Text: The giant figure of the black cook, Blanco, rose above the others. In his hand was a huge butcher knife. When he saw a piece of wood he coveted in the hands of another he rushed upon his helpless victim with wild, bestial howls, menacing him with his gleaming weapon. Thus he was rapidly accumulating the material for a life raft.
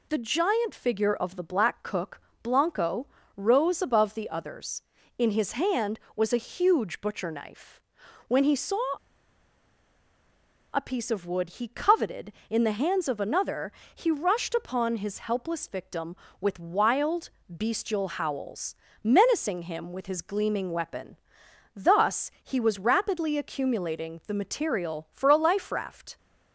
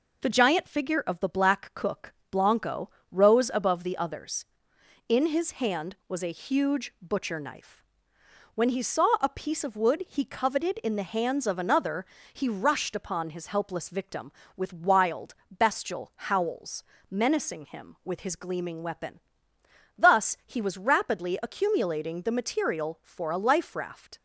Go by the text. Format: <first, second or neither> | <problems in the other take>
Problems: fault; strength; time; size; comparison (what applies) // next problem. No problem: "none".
second | pauses between "saw" and "a"; strong; at 8.8 s; 1.9 s long // pauses between "another" and "he"; slight; at 13.7 s; 0.24 s long; slight in the second